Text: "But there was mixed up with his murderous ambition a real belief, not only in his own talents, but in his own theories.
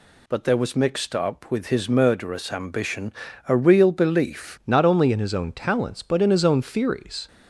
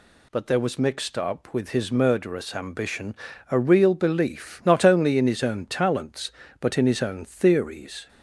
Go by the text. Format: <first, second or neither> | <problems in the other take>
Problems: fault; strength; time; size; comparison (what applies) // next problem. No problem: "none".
second | pauses between "ambition" and "a"; slight; at 3.1 s; 0.36 s long; slight in the second // changes voice at "not"; from 4.6 s on; 2.6 s long